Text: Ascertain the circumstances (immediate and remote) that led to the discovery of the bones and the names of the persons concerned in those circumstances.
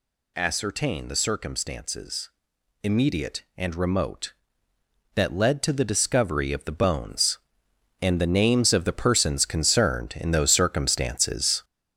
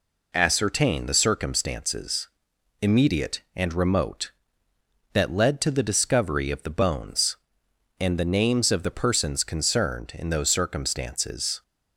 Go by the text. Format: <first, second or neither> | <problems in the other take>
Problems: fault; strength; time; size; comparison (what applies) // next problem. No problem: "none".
second | gets louder; noticeable; throughout; 6 dB